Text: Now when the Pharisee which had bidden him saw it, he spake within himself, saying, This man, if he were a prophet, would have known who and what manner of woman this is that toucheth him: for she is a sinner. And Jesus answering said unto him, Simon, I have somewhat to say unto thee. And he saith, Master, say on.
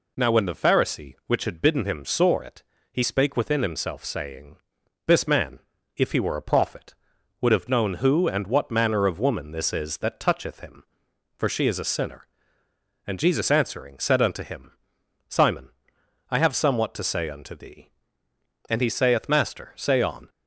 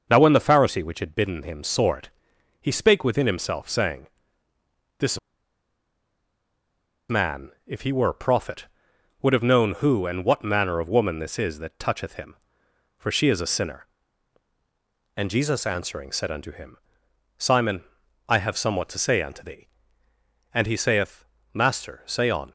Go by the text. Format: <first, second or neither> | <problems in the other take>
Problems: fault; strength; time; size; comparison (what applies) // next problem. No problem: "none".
first | starts louder than the rest; until 1.1 s; 6 dB // pauses between "This" and "man"; strong; at 5.1 s; 1.9 s long